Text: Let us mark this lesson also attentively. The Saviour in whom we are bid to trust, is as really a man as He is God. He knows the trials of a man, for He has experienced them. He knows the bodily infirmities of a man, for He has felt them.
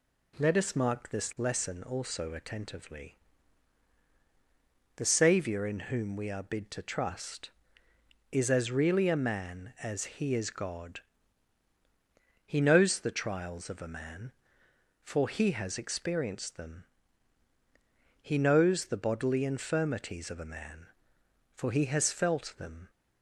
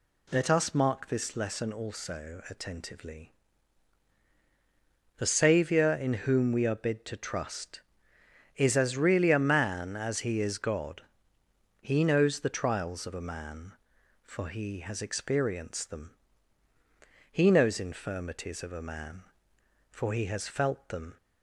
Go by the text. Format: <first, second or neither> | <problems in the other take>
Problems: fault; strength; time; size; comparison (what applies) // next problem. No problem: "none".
first | skips "the bodily"; at 17.7 s